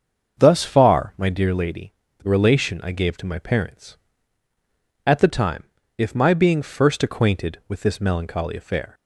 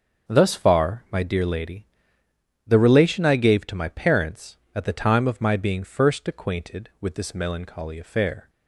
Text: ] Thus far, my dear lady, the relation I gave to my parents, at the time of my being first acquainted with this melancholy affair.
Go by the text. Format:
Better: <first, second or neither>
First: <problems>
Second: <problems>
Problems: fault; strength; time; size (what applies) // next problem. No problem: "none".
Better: second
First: starts louder than the rest; until 1.4 s; 6.5 dB // says "if" for "of"; at 5.9 s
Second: starts louder than the rest; until 1.3 s; 6.5 dB